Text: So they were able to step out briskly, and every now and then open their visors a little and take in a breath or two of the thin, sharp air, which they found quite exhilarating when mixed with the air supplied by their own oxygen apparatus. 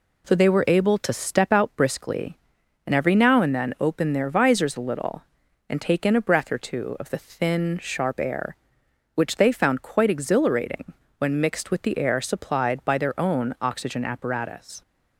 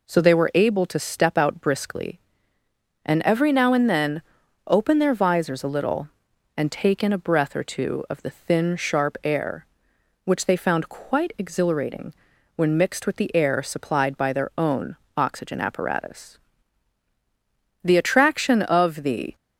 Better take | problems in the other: first | pauses between "then" and "open"; noticeable; at 4.2 s; 0.46 s long // pauses between "exhilarating" and "when"; at 12.1 s; 0.42 s long; slight in the first // pauses between "own" and "oxygen"; slight; at 14.9 s; 0.22 s long // goes on to say "The attraction of the"; from 17.8 s on; 1.5 s long

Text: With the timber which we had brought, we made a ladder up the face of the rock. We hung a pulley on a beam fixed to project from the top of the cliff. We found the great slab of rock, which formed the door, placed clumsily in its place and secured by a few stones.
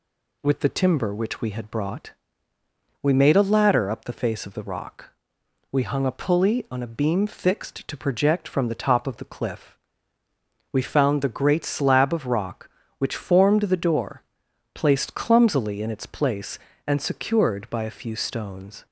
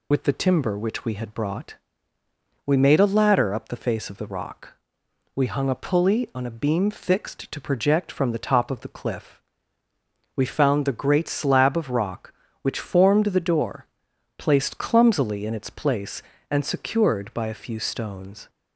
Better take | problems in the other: first | loses the start of "With"; at 0.1 s; 55 ms

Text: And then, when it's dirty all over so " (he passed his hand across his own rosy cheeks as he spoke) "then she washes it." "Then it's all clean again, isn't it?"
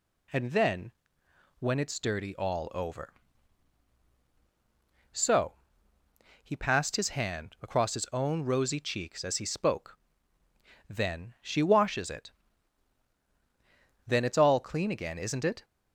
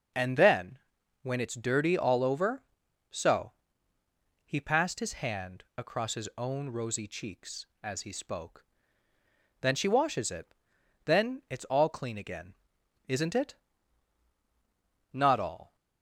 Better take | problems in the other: first | goes on to say "Not all"; noticeable; from 15.1 s on; 0.62 s long

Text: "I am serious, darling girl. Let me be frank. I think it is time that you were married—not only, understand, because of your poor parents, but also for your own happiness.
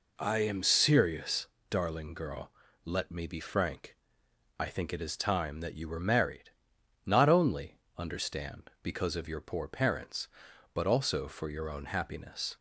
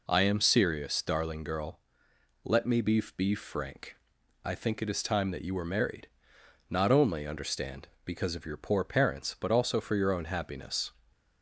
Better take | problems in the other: first | says "be" twice; at 3.1 s

